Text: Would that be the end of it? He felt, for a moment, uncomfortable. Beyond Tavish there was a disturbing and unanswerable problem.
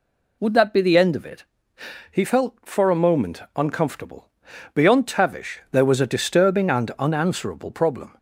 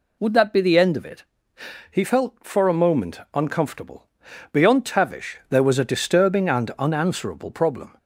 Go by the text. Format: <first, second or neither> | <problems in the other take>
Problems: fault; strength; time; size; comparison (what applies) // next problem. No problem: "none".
neither | none